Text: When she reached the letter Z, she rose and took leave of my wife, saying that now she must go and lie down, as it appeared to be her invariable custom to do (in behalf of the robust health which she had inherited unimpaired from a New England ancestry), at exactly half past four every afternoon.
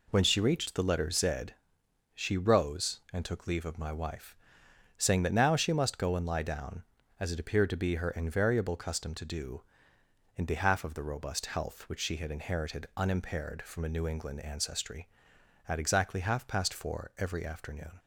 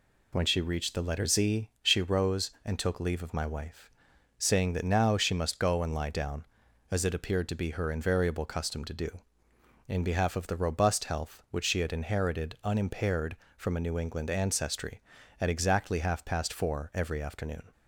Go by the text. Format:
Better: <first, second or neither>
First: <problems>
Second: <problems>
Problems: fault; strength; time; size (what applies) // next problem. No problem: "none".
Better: neither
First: none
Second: none